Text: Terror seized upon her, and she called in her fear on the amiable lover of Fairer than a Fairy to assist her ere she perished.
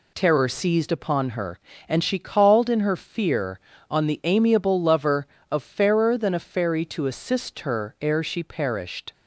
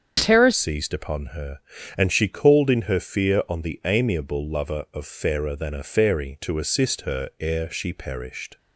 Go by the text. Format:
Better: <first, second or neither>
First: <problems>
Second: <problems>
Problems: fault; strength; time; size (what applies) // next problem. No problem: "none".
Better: first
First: none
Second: starts louder than the rest; strong; until 1.2 s; 7 dB // changes voice at "seized"; from 0.5 s on; 8.0 s long